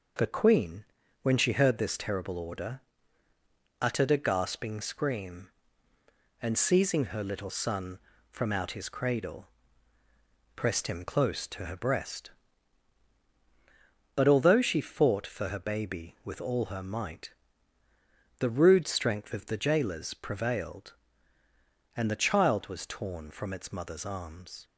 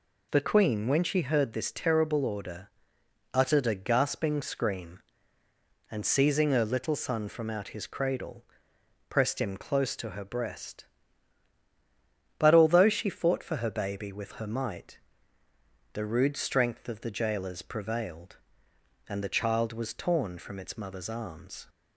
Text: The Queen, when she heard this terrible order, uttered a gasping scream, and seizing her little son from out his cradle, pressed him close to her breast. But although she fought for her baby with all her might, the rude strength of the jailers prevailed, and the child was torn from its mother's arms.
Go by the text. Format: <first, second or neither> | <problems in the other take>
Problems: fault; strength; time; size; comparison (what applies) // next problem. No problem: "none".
first | skips "all"; at 14.3 s